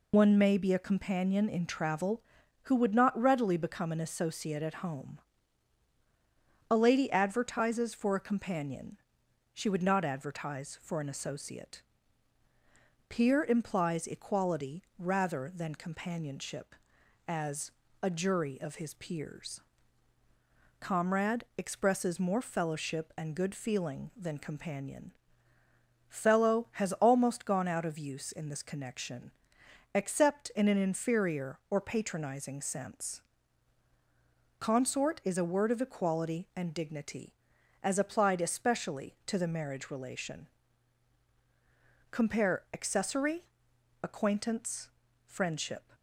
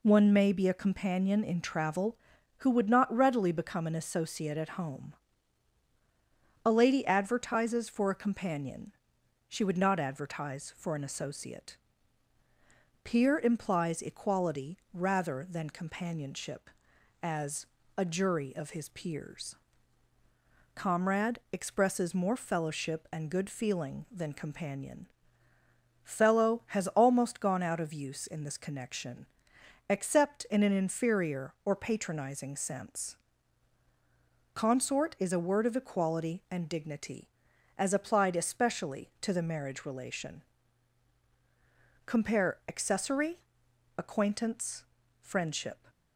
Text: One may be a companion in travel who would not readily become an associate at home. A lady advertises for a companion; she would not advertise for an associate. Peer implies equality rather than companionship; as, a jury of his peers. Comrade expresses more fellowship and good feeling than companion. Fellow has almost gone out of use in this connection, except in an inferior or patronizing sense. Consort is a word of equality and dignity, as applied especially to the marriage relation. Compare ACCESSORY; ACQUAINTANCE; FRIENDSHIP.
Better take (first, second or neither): second